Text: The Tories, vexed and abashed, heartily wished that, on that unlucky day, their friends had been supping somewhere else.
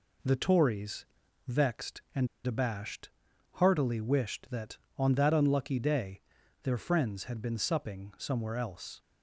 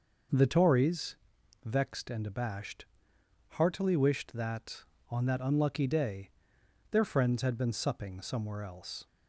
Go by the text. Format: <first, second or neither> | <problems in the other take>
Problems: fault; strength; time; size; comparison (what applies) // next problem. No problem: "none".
second | pauses between "and" and "abashed"; slight; at 2.2 s; 0.18 s long